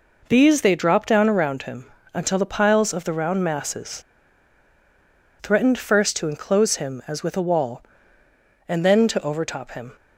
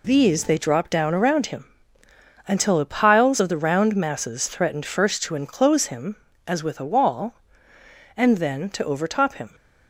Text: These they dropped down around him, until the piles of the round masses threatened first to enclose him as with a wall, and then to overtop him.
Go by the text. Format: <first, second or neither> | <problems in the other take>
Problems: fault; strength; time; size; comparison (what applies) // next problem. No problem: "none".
second | pauses between "masses" and "threatened"; strong; at 4.0 s; 1.3 s long